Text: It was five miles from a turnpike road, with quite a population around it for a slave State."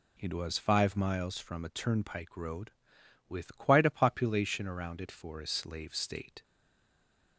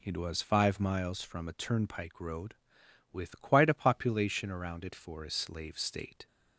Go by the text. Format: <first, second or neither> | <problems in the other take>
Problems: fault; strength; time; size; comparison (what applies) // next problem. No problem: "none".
second | stays silent after the last word; from 6.4 s on; 0.9 s long